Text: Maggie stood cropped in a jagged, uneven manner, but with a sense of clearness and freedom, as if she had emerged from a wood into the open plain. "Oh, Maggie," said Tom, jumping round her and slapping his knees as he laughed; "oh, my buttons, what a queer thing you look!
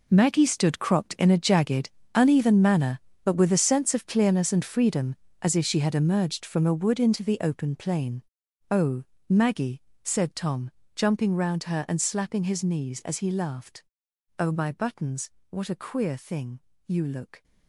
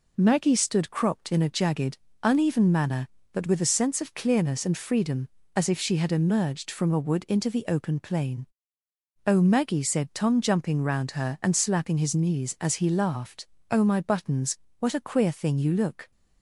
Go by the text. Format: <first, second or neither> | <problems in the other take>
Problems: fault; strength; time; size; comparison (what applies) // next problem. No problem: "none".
second | gets quieter; strong; throughout; 14.5 dB // pauses between "thing" and "you"; slight; at 16.6 s; 0.26 s long